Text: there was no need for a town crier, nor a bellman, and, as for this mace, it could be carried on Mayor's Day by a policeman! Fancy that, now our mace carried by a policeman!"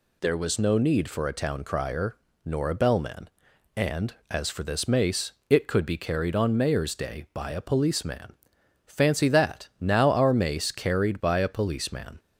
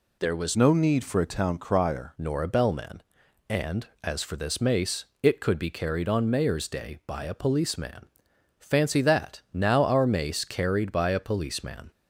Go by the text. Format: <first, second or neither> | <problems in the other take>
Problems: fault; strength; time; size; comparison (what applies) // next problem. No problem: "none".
first | changes voice from "no" to "crier"; from 0.5 to 2.1 s; 1.6 s long